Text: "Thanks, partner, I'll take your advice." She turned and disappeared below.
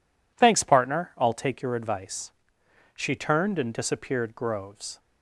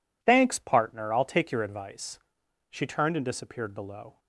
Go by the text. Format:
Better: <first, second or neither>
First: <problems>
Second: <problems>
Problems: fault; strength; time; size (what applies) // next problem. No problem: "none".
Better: second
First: says "groves" for "below"; at 4.3 s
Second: none